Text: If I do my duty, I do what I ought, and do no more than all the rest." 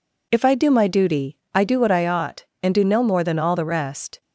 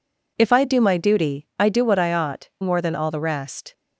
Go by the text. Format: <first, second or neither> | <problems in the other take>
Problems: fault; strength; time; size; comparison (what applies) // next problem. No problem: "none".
first | skips "and do no"; at 2.5 s